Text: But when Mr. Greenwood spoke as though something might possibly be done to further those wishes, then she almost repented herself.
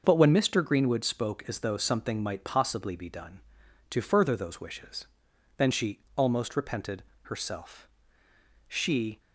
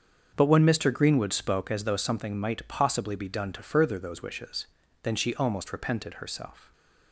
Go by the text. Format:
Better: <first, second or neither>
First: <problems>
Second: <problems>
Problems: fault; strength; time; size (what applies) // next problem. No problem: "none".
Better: second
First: starts louder than the rest; until 1.0 s; 6.5 dB // pauses between "she" and "almost"; slight; at 5.9 s; 0.20 s long // pauses between "repented" and "herself"; slight; at 7.0 s; 0.22 s long // goes on to say "She"; from 8.6 s on; 0.52 s long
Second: starts louder than the rest; until 1.3 s; 7 dB